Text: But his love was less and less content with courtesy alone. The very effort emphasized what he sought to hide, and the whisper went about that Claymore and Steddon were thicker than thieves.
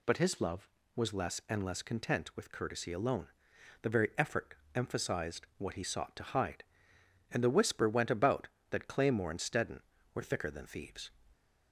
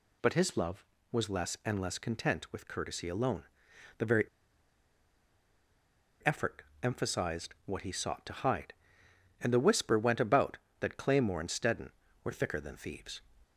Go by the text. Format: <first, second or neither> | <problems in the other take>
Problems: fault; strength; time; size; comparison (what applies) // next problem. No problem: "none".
first | pauses between "very" and "effort"; strong; at 4.2 s; 1.9 s long // pauses between "effort" and "emphasized"; slight; at 6.6 s; 0.22 s long; slight in the first